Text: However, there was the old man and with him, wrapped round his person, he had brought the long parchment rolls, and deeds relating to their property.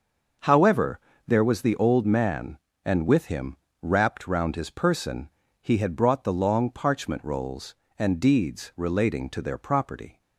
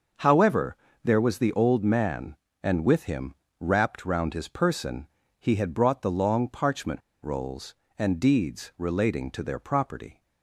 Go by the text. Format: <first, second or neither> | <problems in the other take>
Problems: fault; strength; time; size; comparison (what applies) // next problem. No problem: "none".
first | starts louder than the rest; noticeable; until 1.4 s; 6 dB // pauses between "parchment" and "rolls"; slight; at 6.9 s; 0.22 s long